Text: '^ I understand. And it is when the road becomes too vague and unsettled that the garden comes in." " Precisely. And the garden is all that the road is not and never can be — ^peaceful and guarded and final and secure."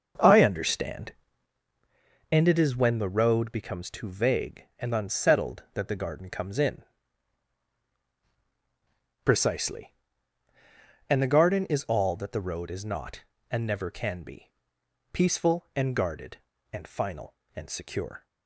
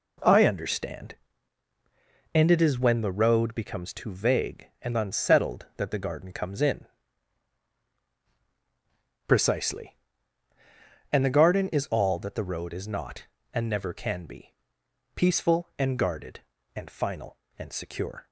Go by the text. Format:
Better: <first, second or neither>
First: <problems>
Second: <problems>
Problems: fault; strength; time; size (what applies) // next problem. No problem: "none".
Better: second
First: starts louder than the rest; until 1.7 s; 7 dB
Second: none